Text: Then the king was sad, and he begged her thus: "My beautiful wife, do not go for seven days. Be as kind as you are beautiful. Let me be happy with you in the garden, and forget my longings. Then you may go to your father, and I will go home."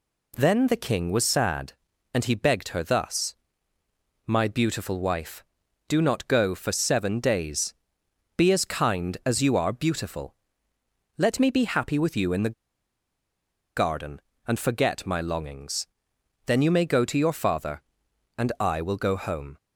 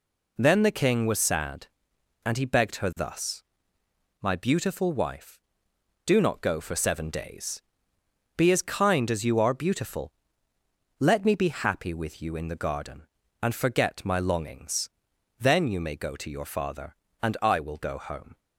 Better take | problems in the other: second | pauses between "the" and "garden"; at 12.5 s; 1.2 s long

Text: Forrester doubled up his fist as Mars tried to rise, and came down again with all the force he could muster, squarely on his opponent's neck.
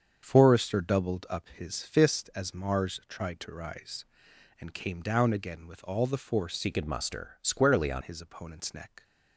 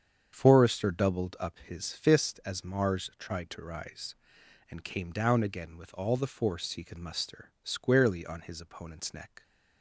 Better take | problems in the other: second | starts louder than the rest; strong; until 1.2 s; 7 dB; strong in the second // changes voice from "he" to "on"; from 6.6 to 8.0 s; 1.4 s long

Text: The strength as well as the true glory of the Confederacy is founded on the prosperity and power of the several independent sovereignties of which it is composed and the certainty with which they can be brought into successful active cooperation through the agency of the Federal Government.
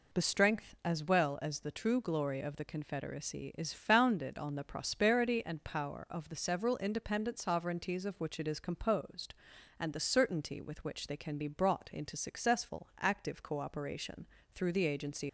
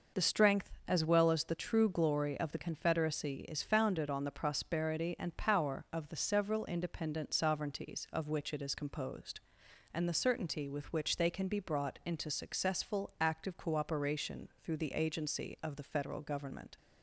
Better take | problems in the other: second | pauses between "cooperation" and "through"; slight; at 14.2 s; 0.30 s long // stops before "of the Federal Government"; at 15.2 s

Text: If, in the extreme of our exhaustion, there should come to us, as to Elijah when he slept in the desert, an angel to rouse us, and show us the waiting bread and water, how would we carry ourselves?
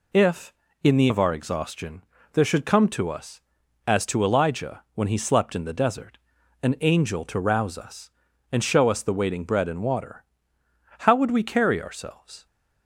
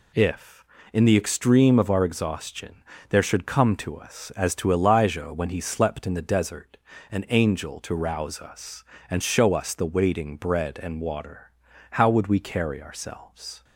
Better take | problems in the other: second | skips "extreme"; at 1.0 s

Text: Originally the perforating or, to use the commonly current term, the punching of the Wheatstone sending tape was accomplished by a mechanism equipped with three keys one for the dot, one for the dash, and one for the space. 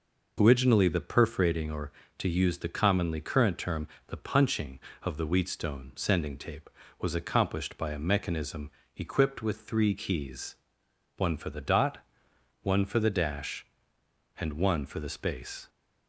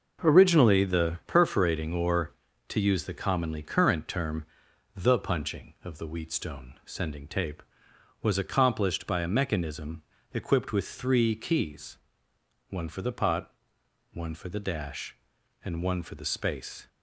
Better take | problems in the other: first | pauses between "mechanism" and "equipped"; slight; at 10.0 s; 0.32 s long; slight in the first // pauses between "keys" and "one"; noticeable; at 11.9 s; 0.72 s long; noticeable in the first // says "pot" for "dot"; at 13.1 s

